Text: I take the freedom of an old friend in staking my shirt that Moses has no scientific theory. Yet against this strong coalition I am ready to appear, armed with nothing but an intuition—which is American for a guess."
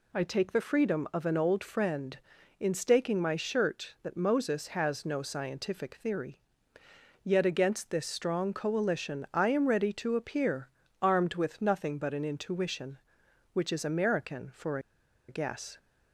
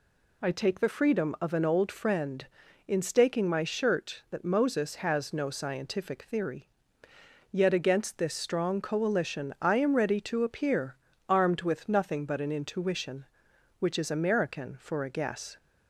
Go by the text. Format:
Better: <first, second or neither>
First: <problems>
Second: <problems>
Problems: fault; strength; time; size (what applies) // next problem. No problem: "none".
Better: second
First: pauses between "for" and "a"; noticeable; at 14.7 s; 0.49 s long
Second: none